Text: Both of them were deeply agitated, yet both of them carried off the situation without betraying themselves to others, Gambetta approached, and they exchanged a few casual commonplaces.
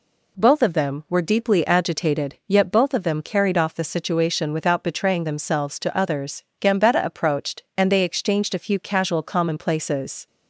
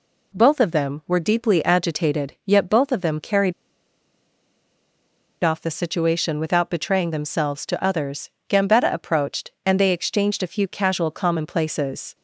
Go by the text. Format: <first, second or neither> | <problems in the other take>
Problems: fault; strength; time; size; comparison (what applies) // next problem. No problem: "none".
first | pauses between "carried" and "off"; strong; at 3.5 s; 1.8 s long